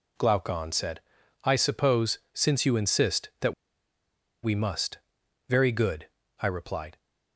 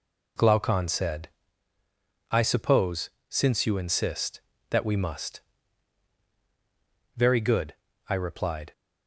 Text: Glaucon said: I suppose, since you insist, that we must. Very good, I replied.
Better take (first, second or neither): second